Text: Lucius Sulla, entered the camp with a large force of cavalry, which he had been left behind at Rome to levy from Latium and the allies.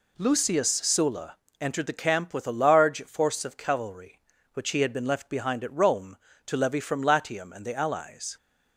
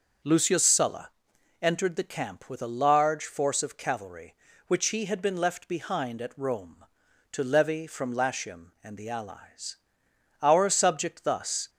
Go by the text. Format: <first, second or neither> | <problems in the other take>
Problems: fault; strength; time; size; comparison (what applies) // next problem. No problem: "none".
first | starts louder than the rest; until 1.7 s; 6.5 dB // goes on to say "Our subject thus"; noticeable; from 10.4 s on; 1.2 s long